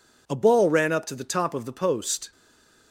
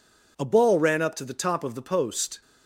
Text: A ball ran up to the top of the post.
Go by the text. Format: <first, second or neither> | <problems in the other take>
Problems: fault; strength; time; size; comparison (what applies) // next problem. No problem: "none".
second | stays silent after the last word; slight; from 2.3 s on; 0.6 s long